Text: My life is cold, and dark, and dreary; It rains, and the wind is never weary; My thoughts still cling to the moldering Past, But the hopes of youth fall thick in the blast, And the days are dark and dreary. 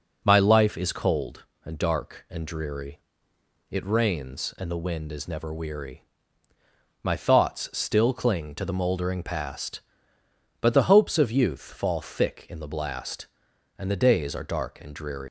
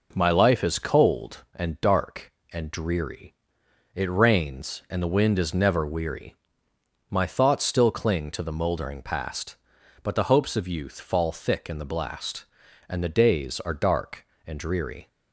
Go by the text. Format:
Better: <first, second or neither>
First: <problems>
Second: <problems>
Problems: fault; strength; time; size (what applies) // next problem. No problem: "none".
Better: second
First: leaves "dreary" unfinished; at 15.2 s; 125 ms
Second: none